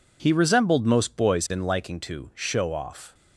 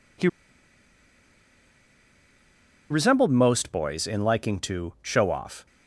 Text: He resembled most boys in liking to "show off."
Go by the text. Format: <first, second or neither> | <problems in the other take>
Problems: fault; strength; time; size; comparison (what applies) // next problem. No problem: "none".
first | pauses between "He" and "resembled"; strong; at 0.2 s; 2.6 s long